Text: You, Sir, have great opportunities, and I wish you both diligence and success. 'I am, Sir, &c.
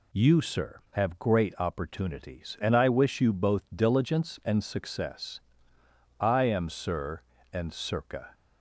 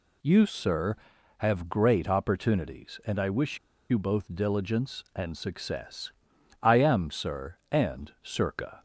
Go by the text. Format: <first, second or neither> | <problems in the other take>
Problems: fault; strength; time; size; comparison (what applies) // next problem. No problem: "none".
first | pauses between "wish" and "you"; slight; at 3.5 s; 0.31 s long